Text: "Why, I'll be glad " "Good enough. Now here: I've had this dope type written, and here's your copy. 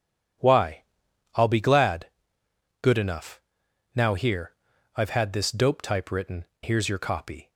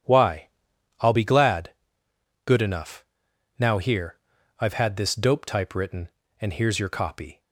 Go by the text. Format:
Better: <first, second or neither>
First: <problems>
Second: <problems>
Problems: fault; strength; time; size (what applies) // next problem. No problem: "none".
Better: second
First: starts louder than the rest; strong; until 1.9 s; 9 dB // skips "and"; at 6.5 s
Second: starts louder than the rest; strong; until 1.5 s; 9 dB